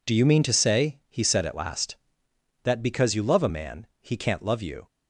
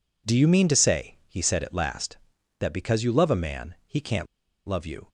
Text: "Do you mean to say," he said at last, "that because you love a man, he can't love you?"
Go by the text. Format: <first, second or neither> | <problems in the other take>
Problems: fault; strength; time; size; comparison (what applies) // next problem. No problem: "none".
first | pauses between "can't" and "love"; at 4.2 s; 0.42 s long